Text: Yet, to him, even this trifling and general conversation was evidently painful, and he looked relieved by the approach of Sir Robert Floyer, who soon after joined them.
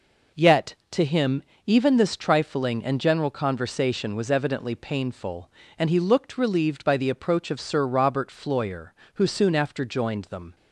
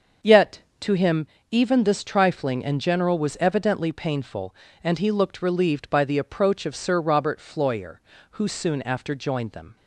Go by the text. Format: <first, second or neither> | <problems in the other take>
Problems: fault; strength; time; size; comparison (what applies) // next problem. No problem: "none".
first | starts louder than the rest; until 1.6 s; 6.5 dB // skips "conversation"; at 3.1 s